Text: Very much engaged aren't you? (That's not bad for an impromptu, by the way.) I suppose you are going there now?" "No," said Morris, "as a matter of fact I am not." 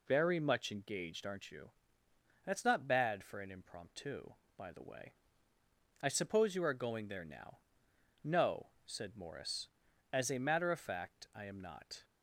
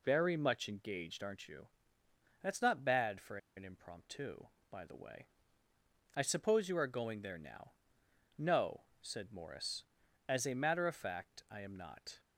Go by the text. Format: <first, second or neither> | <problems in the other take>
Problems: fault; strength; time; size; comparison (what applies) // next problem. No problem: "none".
first | pauses between "for" and "an"; slight; at 3.3 s; 0.18 s long